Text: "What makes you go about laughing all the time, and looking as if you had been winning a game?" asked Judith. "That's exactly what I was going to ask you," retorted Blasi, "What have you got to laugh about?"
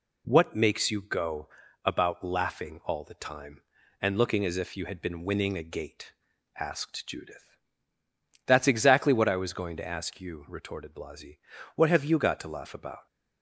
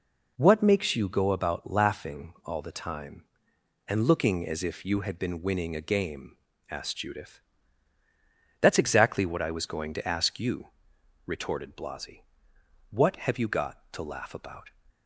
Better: second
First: pauses between "go" and "about"; slight; at 1.4 s; 0.36 s long // says "gate" for "game"; at 5.6 s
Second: none

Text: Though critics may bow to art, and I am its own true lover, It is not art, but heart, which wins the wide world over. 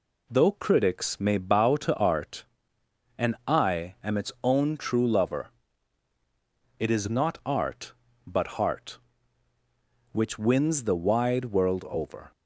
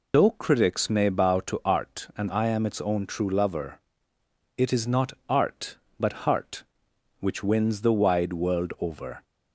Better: first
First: none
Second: loses the start of "Though"; at 0.1 s; 80 ms

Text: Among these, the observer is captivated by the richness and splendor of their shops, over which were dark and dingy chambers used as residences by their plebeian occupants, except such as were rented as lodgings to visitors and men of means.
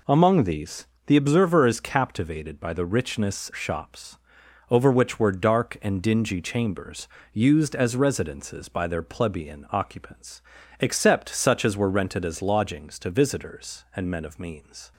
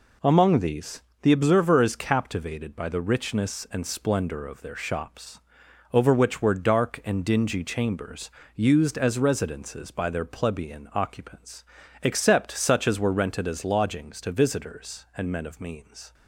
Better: second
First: skips "and splendor of their"; at 3.5 s // pauses between "chambers" and "used"; slight; at 7.0 s; 0.28 s long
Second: pauses between "chambers" and "used"; slight; at 8.2 s; 0.28 s long

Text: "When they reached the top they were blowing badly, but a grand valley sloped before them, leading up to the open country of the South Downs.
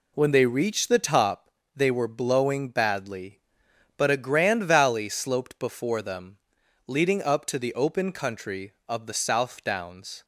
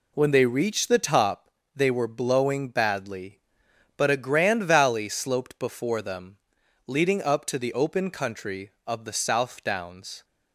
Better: neither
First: pauses between "top" and "they"; slight; at 1.4 s; 0.26 s long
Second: pauses between "top" and "they"; slight; at 1.4 s; 0.26 s long

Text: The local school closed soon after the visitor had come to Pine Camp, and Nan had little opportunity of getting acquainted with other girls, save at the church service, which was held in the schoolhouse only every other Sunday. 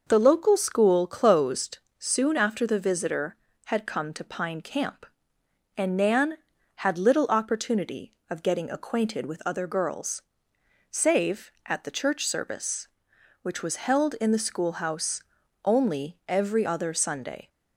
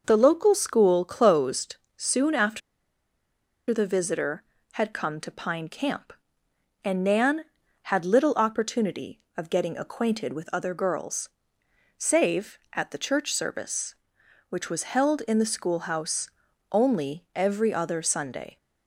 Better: first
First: pauses between "closed" and "soon"; slight; at 1.7 s; 0.20 s long // pauses between "schoolhouse" and "only"; at 15.2 s; 0.40 s long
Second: pauses between "closed" and "soon"; slight; at 1.7 s; 0.20 s long // pauses between "after" and "the"; at 2.6 s; 1.1 s long // pauses between "schoolhouse" and "only"; at 16.3 s; 0.40 s long

